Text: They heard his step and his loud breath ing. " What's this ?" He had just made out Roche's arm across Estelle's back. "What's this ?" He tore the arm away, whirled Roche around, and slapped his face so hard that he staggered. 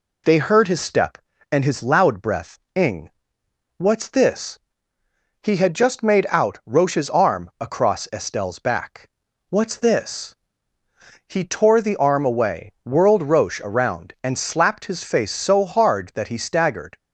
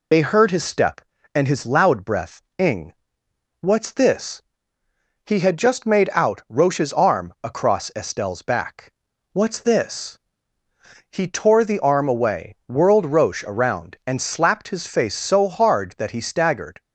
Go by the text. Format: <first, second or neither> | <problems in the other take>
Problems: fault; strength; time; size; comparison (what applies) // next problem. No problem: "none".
first | loses the start of "They"; at 0.1 s; 35 ms // pauses between "breath" and "ing"; slight; at 2.3 s; 0.16 s long; slight in the first